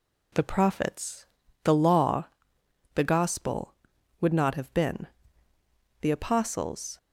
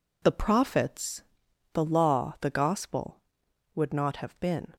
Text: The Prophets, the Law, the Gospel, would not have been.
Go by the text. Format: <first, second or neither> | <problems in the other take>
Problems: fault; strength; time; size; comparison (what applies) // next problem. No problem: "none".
second | goes on to say "The Apostles"; noticeable; from 6.0 s on; 0.96 s long